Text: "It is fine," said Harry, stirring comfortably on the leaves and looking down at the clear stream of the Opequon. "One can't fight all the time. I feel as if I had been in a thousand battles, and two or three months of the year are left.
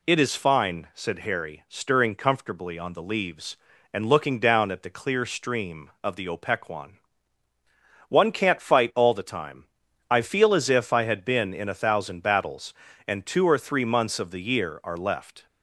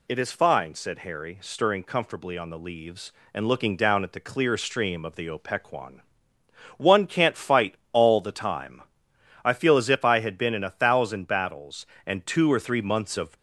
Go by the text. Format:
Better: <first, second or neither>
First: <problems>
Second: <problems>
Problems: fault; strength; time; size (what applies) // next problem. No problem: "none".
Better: first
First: none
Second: pauses between "fight" and "all"; slight; at 7.7 s; 0.16 s long // stops before "the year are left"; at 13.3 s